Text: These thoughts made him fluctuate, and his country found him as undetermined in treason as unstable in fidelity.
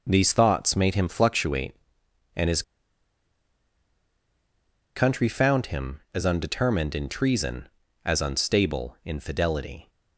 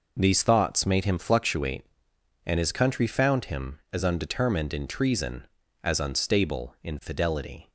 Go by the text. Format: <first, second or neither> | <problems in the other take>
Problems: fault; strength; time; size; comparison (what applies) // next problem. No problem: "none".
second | pauses between "his" and "country"; strong; at 2.6 s; 2.3 s long